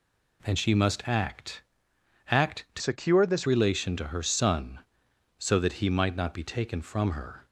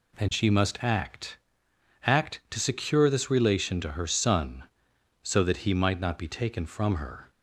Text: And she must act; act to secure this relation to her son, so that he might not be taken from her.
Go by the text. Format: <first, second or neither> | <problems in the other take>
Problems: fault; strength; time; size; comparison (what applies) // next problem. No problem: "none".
second | changes voice from "secure" to "this"; from 2.7 to 3.4 s; 0.7 s long